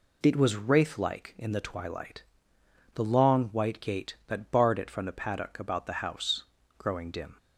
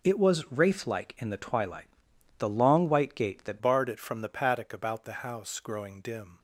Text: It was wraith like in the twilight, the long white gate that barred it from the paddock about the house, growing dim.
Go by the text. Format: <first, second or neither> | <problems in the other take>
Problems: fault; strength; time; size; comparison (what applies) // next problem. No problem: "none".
first | changes voice at "barred"; from 3.6 s on; 2.7 s long